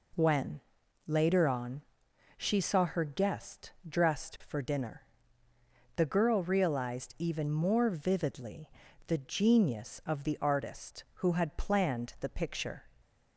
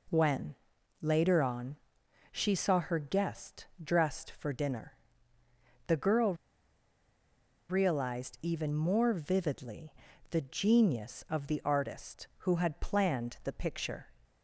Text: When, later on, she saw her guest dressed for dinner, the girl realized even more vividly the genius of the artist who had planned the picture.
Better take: first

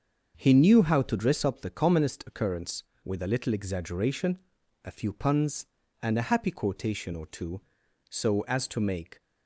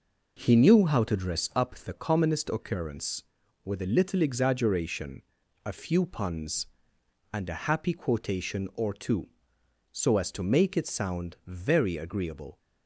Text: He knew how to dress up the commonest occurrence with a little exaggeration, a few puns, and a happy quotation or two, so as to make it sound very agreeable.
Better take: second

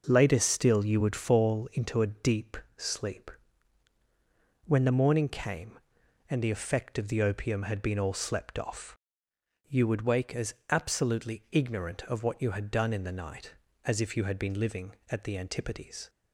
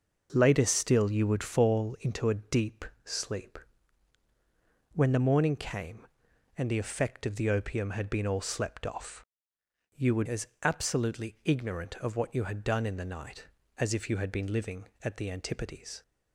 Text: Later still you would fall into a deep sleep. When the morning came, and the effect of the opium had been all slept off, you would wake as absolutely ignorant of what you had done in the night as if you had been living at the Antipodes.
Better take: first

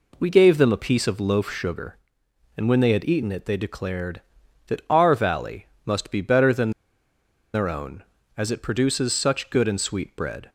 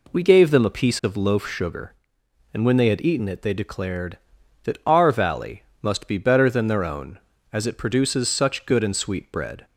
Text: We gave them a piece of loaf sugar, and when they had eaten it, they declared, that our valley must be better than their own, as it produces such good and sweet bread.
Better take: second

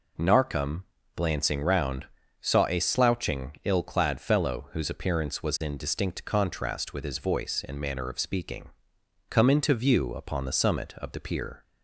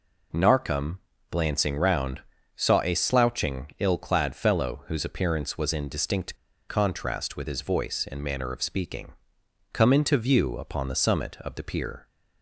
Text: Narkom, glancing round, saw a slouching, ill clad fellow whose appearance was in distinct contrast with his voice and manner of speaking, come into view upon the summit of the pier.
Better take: first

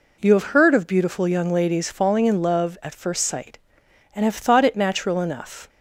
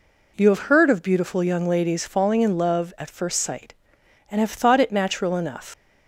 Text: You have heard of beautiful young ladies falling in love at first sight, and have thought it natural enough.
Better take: first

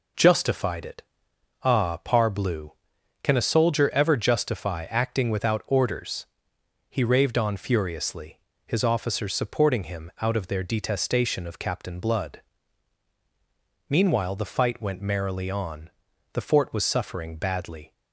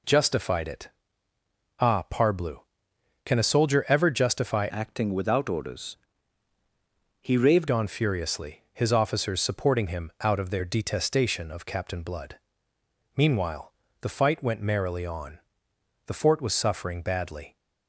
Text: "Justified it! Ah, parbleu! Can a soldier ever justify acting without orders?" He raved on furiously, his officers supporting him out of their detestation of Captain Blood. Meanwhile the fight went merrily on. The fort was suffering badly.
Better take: first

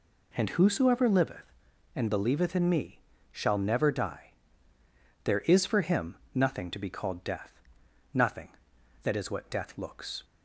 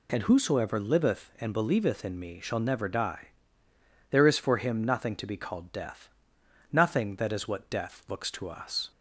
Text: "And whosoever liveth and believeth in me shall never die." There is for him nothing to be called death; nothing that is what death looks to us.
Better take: second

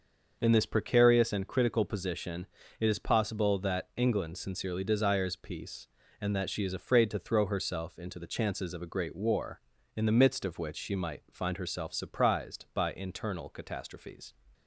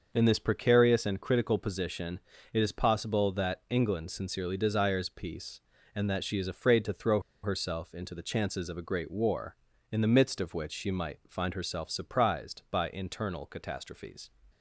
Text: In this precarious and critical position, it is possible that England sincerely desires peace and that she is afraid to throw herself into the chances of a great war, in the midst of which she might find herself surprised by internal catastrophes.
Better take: first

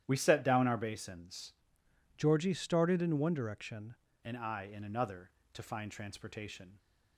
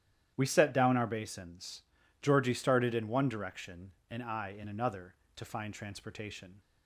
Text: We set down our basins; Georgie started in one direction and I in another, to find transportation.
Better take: second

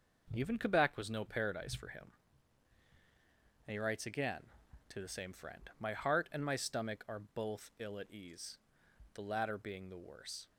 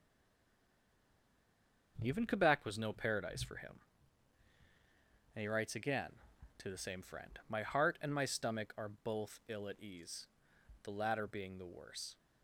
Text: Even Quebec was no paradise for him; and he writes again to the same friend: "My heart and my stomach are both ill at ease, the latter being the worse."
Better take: first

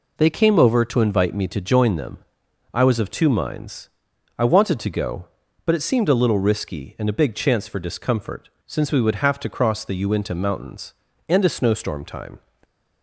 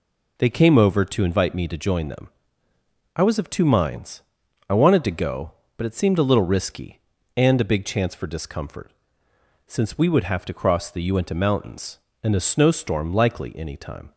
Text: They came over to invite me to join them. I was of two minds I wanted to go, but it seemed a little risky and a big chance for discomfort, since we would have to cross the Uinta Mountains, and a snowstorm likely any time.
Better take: second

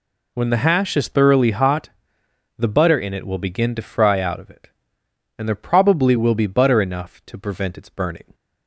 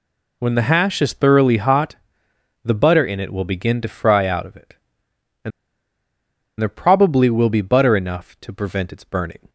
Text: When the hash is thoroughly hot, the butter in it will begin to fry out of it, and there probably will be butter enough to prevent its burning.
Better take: first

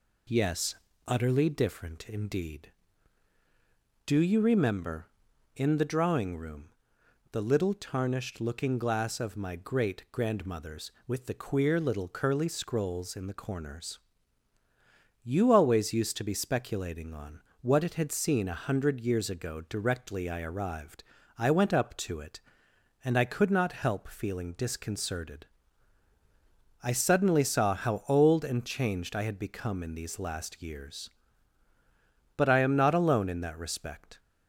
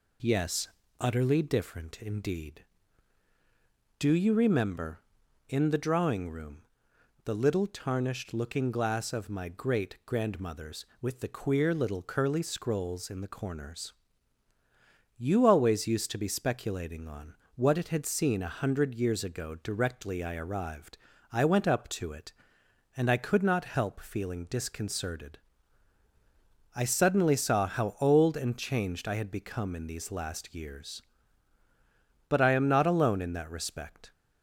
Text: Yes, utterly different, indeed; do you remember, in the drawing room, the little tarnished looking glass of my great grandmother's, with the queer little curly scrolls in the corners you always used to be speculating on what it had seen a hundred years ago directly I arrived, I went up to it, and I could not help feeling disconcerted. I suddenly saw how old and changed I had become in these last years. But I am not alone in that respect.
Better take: neither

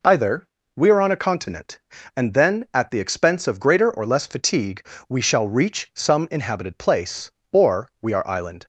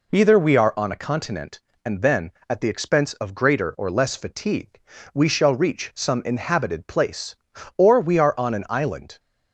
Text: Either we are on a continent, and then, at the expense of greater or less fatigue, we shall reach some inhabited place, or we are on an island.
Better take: second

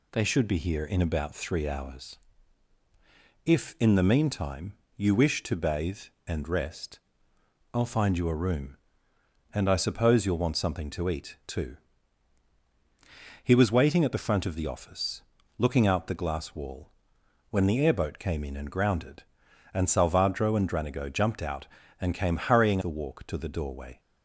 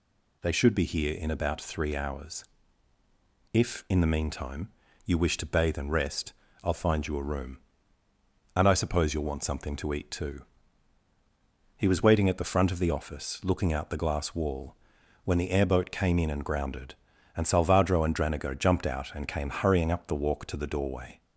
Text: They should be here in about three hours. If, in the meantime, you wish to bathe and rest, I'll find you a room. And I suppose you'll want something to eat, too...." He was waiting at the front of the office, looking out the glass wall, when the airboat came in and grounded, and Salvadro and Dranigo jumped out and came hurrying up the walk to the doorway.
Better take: second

